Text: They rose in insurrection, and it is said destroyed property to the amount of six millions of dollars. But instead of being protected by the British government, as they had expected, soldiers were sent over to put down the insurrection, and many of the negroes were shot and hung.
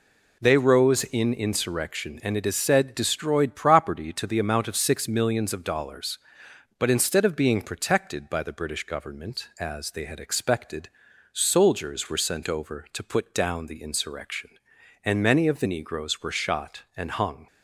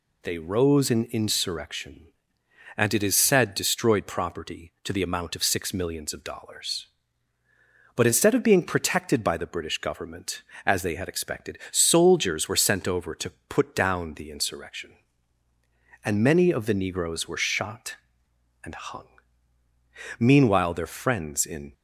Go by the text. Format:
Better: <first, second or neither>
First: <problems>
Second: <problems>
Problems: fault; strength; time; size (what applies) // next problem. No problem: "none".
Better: first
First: none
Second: pauses between "to" and "put"; slight; at 13.3 s; 0.16 s long // goes on to say "Meanwhile their friends in"; from 20.2 s on; 1.5 s long